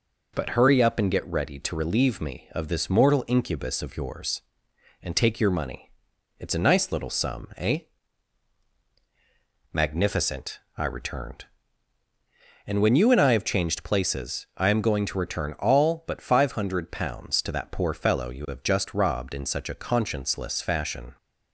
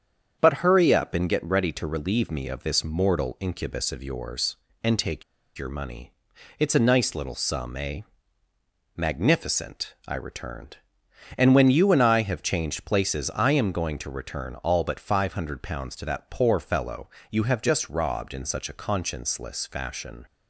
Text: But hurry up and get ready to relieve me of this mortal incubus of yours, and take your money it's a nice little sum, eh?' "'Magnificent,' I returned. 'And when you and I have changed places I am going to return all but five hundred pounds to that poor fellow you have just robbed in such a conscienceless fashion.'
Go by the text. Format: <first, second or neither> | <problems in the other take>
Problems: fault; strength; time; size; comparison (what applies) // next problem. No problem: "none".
first | starts louder than the rest; strong; until 1.4 s; 7.5 dB // pauses between "take" and "your"; slight; at 5.2 s; 0.35 s long // pauses between "money" and "it's"; noticeable; at 6.1 s; 0.46 s long; noticeable in the first // pauses between "fellow" and "you"; slight; at 17.1 s; 0.20 s long